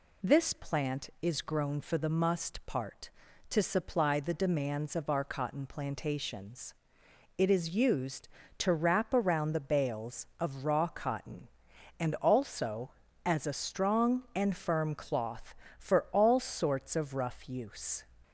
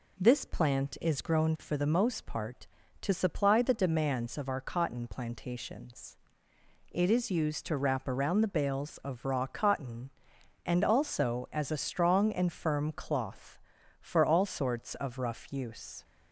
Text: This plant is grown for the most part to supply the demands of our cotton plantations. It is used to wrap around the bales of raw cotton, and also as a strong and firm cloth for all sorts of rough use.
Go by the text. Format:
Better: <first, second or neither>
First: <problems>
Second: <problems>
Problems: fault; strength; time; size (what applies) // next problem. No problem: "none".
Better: second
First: says "must" for "most"; at 2.0 s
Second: none